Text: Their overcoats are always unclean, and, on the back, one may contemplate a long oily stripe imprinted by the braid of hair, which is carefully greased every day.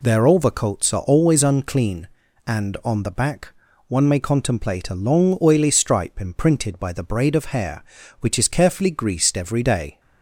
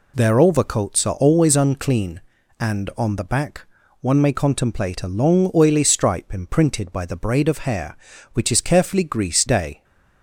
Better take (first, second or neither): first